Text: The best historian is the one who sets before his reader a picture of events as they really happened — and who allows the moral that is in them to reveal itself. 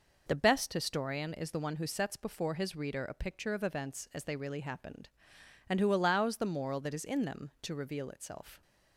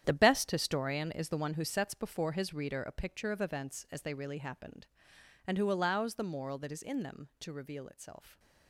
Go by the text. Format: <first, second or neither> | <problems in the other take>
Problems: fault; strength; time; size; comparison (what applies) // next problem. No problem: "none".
first | gets quieter; strong; throughout; 11.5 dB